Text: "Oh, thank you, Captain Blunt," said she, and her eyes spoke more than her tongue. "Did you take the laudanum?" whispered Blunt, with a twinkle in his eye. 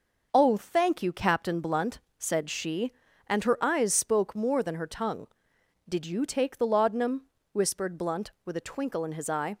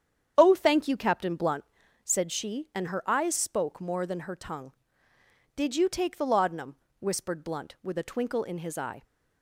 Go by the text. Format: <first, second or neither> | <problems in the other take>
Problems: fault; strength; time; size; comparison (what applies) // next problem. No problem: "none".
first | starts louder than the rest; strong; until 2.1 s; 8.5 dB